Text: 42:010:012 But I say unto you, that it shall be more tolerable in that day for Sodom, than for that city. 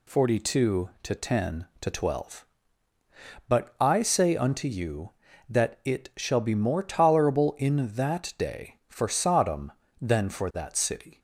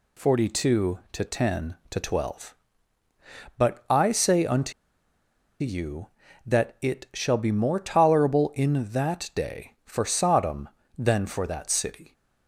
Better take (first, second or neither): first